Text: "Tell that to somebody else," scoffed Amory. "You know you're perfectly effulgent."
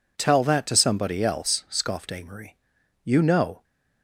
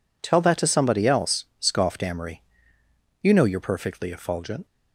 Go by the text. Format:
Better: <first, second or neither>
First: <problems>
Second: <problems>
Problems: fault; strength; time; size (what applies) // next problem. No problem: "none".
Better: second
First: stops before "you're perfectly effulgent"; at 3.6 s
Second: none